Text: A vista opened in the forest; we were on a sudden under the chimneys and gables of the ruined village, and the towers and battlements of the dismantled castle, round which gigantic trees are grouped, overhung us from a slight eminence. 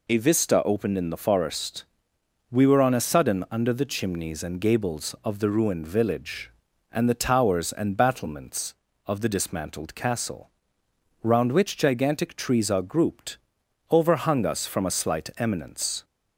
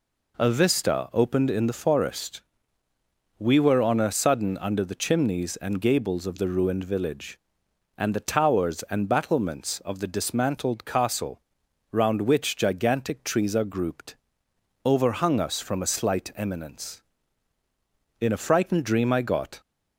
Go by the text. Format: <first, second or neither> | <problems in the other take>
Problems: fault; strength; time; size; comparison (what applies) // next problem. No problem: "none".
first | goes on to say "In a frightened dream I got"; from 18.2 s on; 1.4 s long